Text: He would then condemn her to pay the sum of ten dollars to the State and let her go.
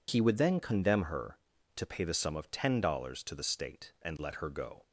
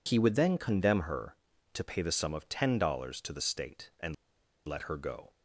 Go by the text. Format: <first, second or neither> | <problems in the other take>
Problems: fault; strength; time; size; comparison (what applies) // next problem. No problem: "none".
first | pauses between "and" and "let"; noticeable; at 4.1 s; 0.51 s long